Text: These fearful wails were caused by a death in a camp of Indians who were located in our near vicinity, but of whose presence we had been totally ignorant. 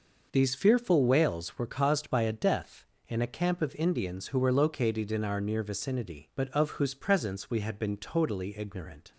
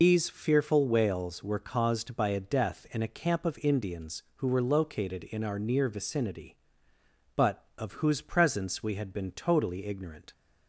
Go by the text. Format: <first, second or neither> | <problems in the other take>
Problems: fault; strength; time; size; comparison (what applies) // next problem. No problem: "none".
first | loses the start of "These"; at 0.0 s; 85 ms